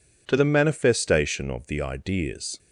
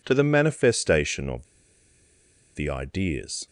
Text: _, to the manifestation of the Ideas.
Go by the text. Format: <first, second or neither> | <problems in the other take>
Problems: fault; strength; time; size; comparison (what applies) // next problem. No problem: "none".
first | pauses between "of" and "the"; at 1.4 s; 1.0 s long